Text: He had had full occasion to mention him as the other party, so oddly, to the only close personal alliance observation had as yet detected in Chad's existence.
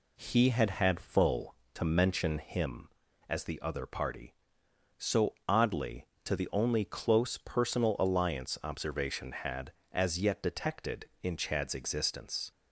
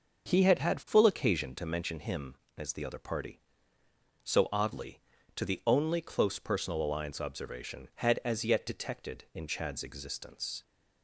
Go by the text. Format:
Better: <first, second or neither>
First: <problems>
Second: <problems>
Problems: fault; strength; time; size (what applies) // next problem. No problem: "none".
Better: second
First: skips "occasion"; at 1.6 s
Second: none